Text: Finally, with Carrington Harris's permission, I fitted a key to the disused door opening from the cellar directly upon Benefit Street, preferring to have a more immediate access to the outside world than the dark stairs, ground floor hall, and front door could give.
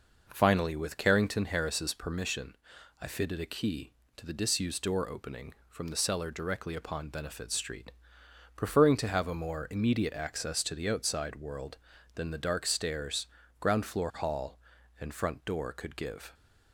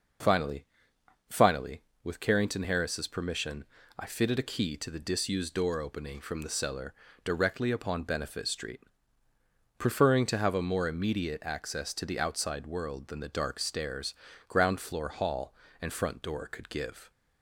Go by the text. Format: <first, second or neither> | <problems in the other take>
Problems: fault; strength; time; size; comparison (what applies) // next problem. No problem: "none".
first | says "Finally" twice; at 1.2 s // pauses between "cellar" and "directly"; slight; at 6.9 s; 0.32 s long